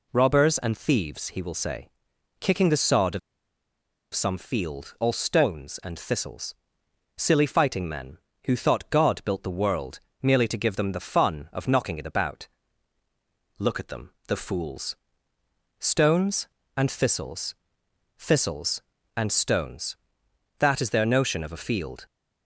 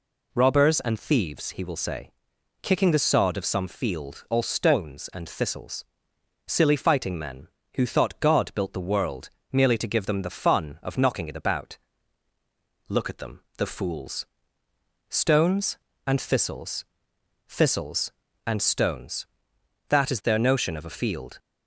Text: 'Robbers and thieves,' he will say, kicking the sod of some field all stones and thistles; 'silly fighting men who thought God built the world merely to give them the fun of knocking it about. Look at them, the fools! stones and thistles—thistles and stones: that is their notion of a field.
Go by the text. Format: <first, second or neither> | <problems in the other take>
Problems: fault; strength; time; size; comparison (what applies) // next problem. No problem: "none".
second | pauses between "of" and "some"; noticeable; at 3.1 s; 0.94 s long // pauses between "world" and "merely"; slight; at 10.0 s; 0.20 s long; slight in the second